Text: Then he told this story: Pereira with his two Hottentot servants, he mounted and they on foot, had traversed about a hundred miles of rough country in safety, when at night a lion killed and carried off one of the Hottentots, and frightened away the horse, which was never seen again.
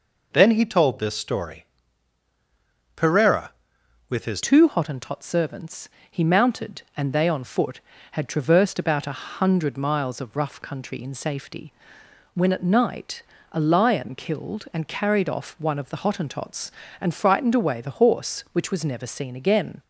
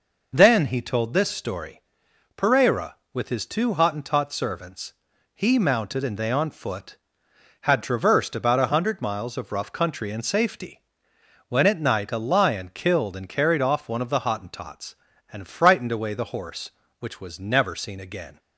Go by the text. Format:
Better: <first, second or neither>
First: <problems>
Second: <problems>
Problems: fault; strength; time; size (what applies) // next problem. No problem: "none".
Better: second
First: changes voice at "two"; from 4.4 s on; 15.4 s long // pauses between "night" and "a"; slight; at 13.2 s; 0.26 s long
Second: none